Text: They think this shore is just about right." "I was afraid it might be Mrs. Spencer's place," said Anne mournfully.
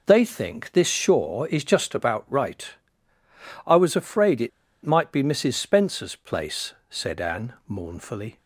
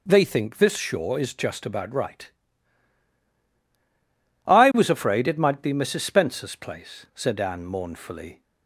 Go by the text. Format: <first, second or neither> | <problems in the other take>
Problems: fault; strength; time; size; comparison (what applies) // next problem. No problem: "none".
second | pauses between "it" and "might"; slight; at 4.4 s; 0.35 s long // pauses between "Anne" and "mournfully"; slight; at 7.5 s; 0.16 s long